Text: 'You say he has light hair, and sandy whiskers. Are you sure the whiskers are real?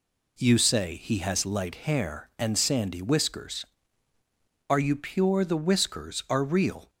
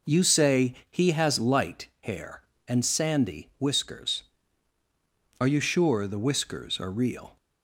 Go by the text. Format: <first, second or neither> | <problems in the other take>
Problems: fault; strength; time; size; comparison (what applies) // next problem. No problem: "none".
second | says "pure" for "sure"; at 4.9 s